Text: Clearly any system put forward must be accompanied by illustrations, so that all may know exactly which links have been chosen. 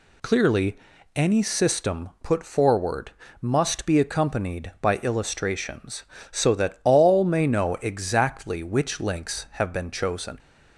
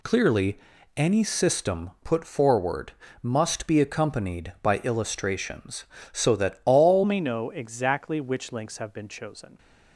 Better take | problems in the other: first | pauses between "Clearly" and "any"; at 0.5 s; 0.38 s long; also in the first // pauses between "forward" and "must"; slight; at 2.9 s; 0.30 s long; slight in the first // changes voice at "may"; from 7.0 s on; 2.5 s long

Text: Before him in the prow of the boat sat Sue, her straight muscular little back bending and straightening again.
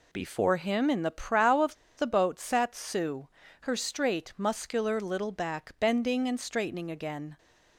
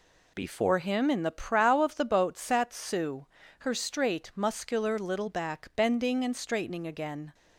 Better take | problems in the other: second | pauses between "of" and "the"; slight; at 1.7 s; 0.22 s long

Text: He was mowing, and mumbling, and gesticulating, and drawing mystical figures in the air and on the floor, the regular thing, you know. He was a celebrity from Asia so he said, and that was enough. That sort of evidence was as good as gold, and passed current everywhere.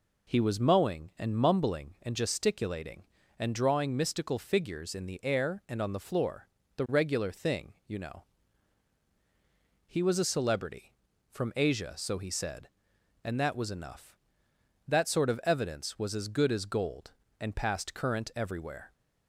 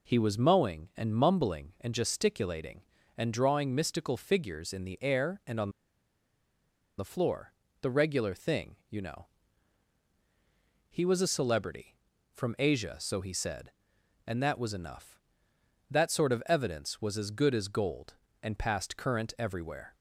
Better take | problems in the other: first | pauses between "on" and "the"; strong; at 5.7 s; 1.2 s long

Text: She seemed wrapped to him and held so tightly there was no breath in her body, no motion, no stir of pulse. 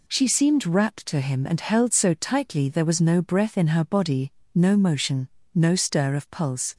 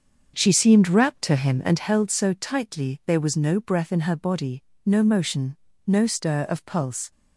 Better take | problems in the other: first | starts louder than the rest; until 1.9 s; 6.5 dB

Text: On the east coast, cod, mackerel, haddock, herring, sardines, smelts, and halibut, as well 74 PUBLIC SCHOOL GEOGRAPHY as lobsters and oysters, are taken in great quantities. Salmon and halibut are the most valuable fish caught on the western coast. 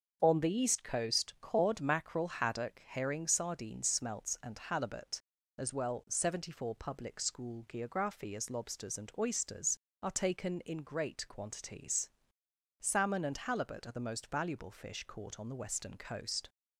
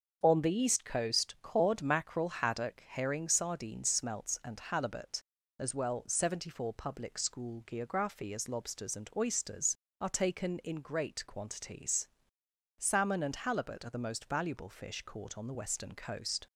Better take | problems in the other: neither | starts louder than the rest; the same in both

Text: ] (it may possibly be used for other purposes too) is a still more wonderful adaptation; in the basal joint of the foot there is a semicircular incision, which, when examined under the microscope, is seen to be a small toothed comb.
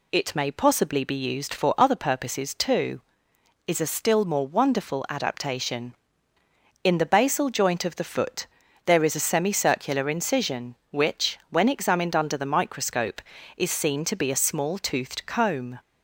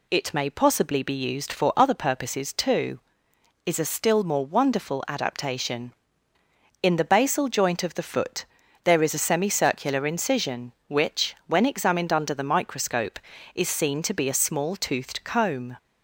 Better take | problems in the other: neither | pauses between "foot" and "there"; the same in both

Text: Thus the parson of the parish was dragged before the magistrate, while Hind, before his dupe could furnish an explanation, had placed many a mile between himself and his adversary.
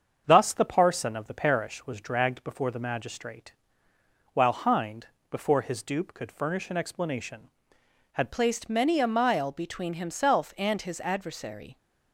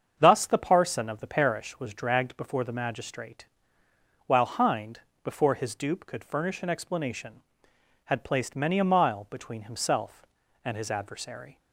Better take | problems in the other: second | starts louder than the rest; until 1.2 s; 7 dB; also in the second // changes voice at "placed"; from 8.3 s on; 3.4 s long

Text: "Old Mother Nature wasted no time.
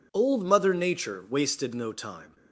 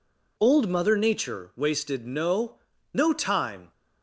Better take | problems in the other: first | says "no" twice; at 2.9 s

